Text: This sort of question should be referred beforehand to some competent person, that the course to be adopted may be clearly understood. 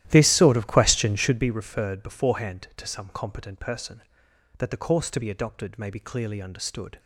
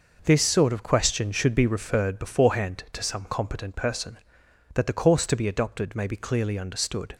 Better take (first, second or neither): second